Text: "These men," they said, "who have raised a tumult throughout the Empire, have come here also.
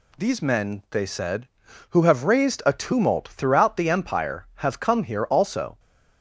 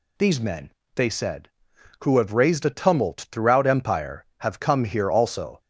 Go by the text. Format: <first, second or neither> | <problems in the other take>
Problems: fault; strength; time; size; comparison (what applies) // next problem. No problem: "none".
first | skips "the"; at 3.6 s